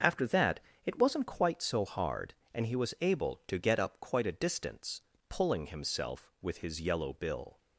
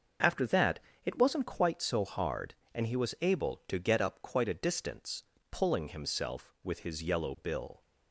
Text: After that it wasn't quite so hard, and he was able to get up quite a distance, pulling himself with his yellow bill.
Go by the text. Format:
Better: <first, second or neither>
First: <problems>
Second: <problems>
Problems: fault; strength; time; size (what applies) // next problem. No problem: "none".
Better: neither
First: starts louder than the rest; noticeable; until 1.3 s; 6 dB // pauses between "that" and "it"; slight; at 0.5 s; 0.26 s long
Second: starts louder than the rest; until 1.4 s; 6.5 dB // pauses between "that" and "it"; slight; at 0.7 s; 0.26 s long